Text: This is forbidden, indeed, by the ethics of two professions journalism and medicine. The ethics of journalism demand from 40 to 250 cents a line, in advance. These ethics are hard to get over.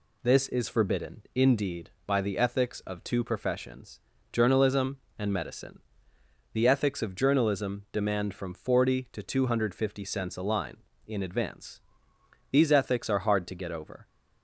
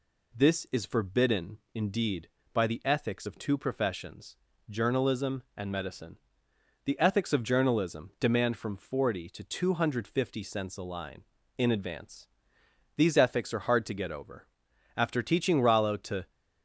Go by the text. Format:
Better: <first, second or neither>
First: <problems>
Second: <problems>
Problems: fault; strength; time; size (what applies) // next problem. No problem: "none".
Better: first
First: pauses between "professions" and "journalism"; slight; at 3.9 s; 0.32 s long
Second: pauses between "professions" and "journalism"; slight; at 4.3 s; 0.32 s long // goes on to say "After teaching Rollo to"; from 14.9 s on; 1.3 s long